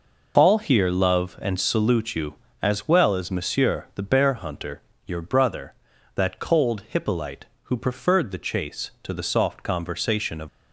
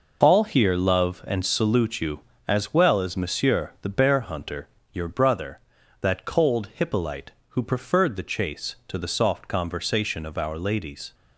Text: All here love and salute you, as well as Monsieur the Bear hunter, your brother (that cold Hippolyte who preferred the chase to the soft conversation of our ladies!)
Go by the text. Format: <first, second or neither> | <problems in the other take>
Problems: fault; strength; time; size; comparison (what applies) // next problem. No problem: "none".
second | stops before "our ladies"; at 10.4 s